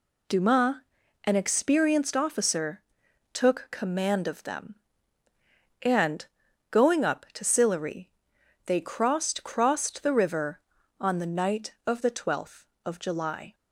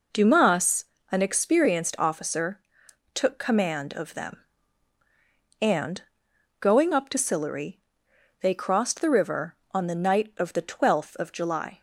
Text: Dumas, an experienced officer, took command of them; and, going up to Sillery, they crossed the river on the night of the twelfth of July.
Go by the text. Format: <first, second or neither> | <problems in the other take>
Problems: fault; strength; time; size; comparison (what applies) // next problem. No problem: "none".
second | says "crossed" twice; at 9.4 s